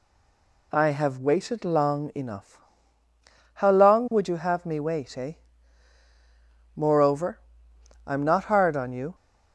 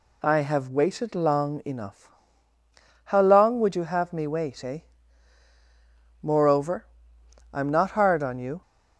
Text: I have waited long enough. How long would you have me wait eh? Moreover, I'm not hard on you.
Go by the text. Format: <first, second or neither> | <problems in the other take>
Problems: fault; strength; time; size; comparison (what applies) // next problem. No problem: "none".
second | stays silent before the first word; slight; until 0.7 s; 0.7 s long